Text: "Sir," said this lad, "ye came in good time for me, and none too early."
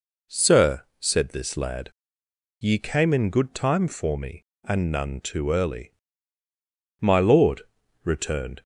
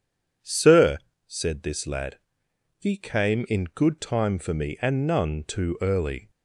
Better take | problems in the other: second | goes on to say "My lord returned"; from 6.9 s on; 1.6 s long

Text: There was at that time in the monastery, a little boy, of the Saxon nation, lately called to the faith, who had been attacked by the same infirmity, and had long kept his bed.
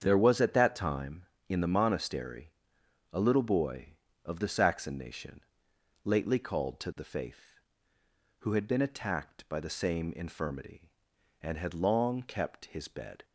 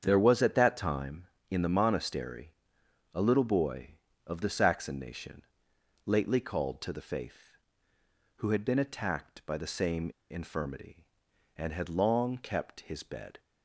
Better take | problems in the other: first | starts louder than the rest; strong; until 1.0 s; 7.5 dB; strong in the first // pauses between "same" and "infirmity"; slight; at 10.0 s; 0.20 s long

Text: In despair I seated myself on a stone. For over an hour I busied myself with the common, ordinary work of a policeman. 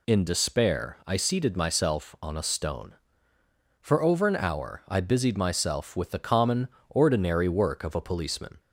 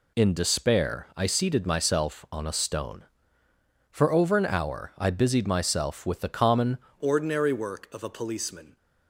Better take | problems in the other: first | changes voice at "ordinary"; from 7.0 s on; 1.7 s long

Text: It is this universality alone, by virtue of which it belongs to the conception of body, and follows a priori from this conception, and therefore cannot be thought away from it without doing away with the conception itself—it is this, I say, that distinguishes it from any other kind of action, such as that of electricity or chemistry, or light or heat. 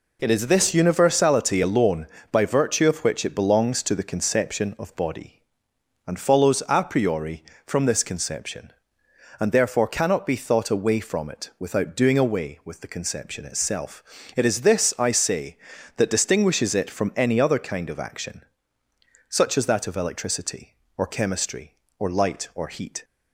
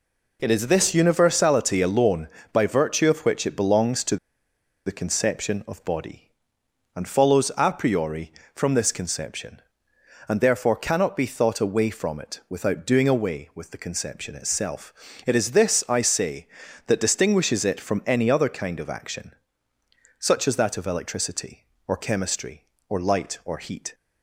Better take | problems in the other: first | pauses between "to" and "the"; noticeable; at 4.1 s; 0.69 s long

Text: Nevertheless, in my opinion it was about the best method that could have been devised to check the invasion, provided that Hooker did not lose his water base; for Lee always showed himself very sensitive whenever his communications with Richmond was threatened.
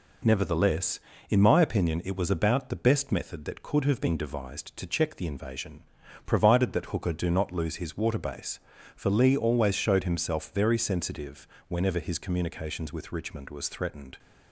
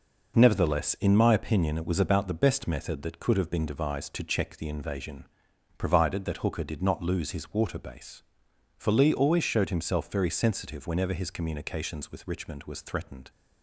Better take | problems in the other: second | says "do" for "did"; at 7.1 s // pauses between "sensitive" and "whenever"; slight; at 11.4 s; 0.22 s long

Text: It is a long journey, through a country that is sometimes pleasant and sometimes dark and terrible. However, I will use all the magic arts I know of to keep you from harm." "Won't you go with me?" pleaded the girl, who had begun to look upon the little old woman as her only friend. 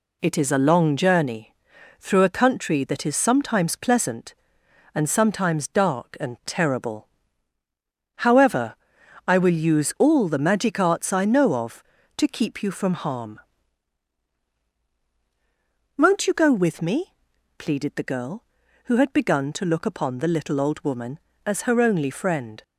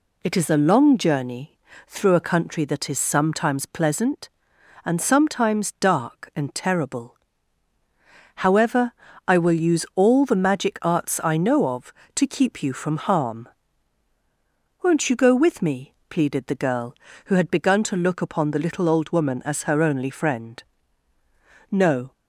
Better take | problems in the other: first | goes on to say "No"; slight; from 21.7 s on; 0.40 s long

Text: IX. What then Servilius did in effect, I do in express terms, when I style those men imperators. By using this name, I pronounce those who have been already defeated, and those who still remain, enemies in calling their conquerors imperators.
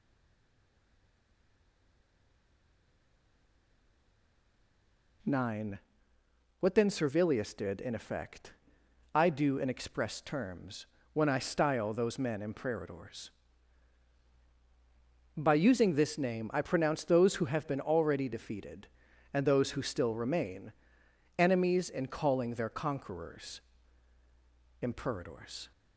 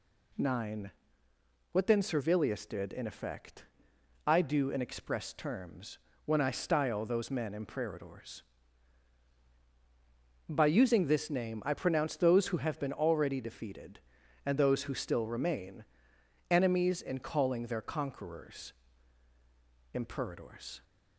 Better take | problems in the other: second | stays silent before the first word; strong; until 5.2 s; 5.2 s long // pauses between "conquerors" and "imperators"; at 23.6 s; 1.2 s long; also in the second

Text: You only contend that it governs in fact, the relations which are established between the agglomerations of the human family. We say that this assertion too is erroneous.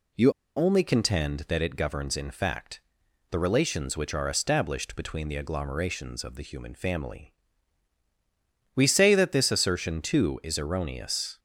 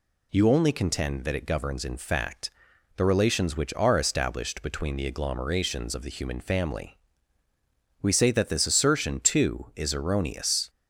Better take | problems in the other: second | pauses between "You" and "only"; slight; at 0.3 s; 0.25 s long

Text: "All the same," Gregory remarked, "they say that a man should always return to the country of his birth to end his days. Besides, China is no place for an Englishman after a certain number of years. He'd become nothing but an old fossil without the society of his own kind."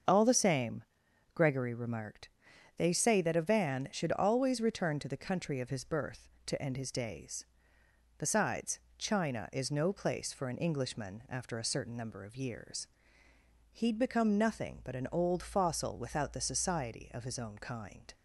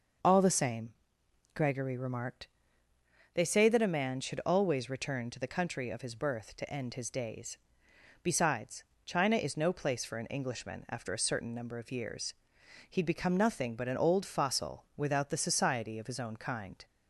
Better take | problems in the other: second | starts louder than the rest; until 1.5 s; 6.5 dB // says "van" for "man"; at 3.4 s

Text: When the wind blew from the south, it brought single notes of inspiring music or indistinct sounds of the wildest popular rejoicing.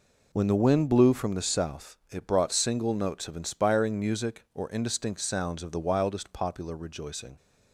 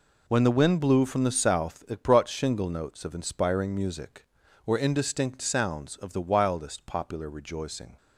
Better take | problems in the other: first | says "shingle" for "single"; at 2.2 s

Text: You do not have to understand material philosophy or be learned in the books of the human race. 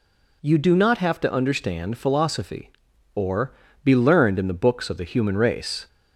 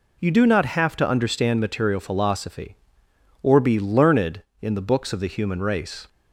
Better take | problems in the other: second | skips "material"; at 1.9 s // pauses between "or" and "be"; slight; at 3.5 s; 0.28 s long

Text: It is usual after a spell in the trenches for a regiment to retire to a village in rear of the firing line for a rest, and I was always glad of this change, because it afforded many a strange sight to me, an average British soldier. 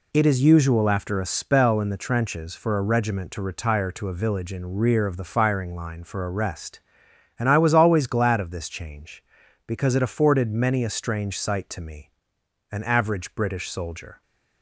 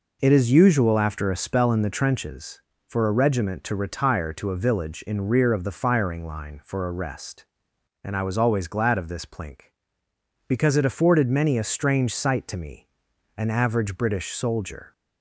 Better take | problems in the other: first | says "plink" for "change"; at 9.2 s

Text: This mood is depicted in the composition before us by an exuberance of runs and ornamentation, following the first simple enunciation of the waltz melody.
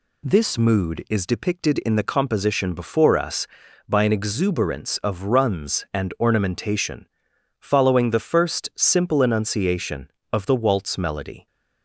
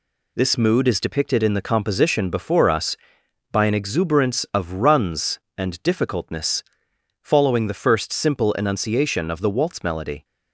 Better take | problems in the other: first | says "difficultness" for "ornamentation"; at 5.8 s

